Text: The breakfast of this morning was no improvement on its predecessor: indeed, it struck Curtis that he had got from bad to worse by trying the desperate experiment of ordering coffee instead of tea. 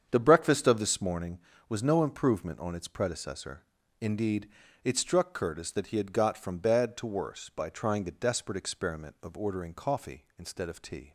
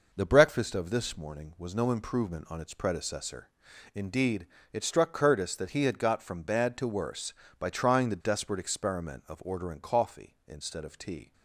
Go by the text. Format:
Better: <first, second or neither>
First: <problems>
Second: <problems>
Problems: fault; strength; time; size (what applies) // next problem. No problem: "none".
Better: second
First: starts louder than the rest; strong; until 1.3 s; 7.5 dB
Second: none